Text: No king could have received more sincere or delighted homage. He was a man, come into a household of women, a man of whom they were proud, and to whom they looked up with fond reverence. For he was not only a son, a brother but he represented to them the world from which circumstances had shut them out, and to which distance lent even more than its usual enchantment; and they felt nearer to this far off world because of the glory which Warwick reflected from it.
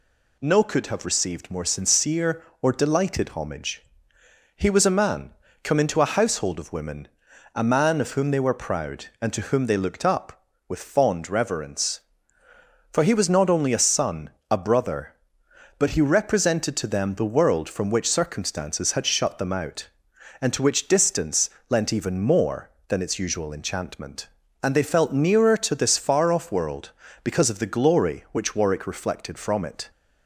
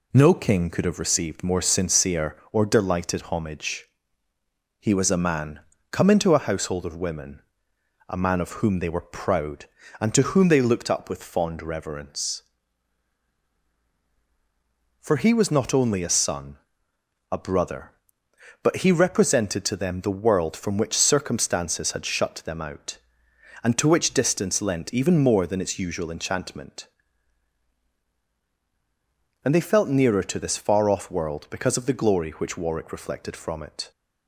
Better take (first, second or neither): second